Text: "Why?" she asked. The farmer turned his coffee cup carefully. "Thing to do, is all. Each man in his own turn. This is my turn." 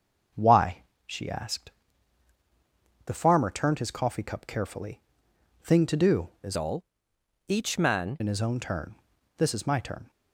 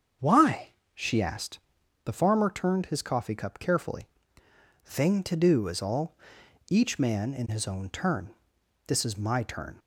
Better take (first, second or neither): second